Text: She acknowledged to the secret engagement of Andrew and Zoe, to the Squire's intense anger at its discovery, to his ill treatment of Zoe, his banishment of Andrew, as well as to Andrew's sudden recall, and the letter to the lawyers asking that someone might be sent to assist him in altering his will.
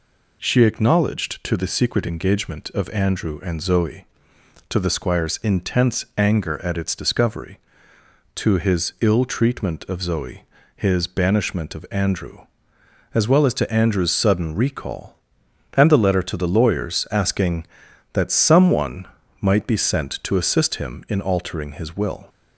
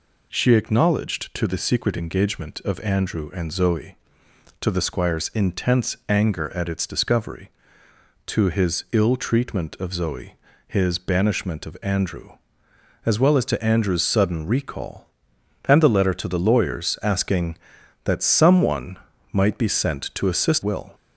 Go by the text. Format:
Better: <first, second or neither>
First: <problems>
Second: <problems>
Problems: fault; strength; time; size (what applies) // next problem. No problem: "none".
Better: first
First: pauses between "someone" and "might"; slight; at 19.0 s; 0.32 s long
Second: pauses between "someone" and "might"; slight; at 18.9 s; 0.32 s long // skips "him in altering his"; at 20.6 s